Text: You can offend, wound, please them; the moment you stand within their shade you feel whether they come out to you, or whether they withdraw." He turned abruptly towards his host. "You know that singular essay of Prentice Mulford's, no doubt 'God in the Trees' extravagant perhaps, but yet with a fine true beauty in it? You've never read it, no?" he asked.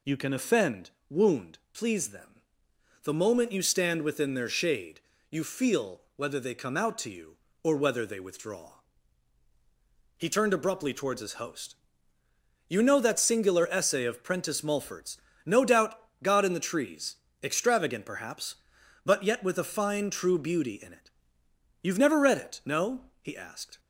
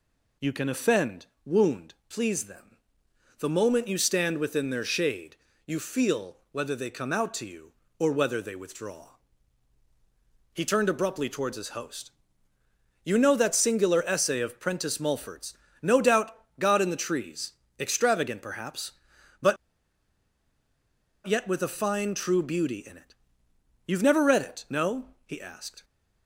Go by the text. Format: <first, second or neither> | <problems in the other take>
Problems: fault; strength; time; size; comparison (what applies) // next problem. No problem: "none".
first | pauses between "shade" and "you"; slight; at 5.3 s; 0.28 s long; slight in the first // pauses between "feel" and "whether"; slight; at 6.3 s; 0.16 s long; slight in the first // pauses between "doubt" and "God"; slight; at 16.3 s; 0.22 s long; slight in the first // pauses between "Trees" and "extravagant"; slight; at 17.5 s; 0.28 s long; slight in the first // pauses between "but" and "yet"; strong; at 19.5 s; 1.6 s long